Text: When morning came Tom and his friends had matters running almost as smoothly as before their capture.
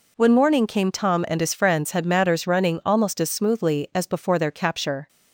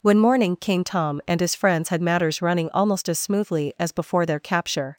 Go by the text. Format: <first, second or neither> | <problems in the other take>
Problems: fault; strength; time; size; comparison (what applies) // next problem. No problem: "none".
neither | none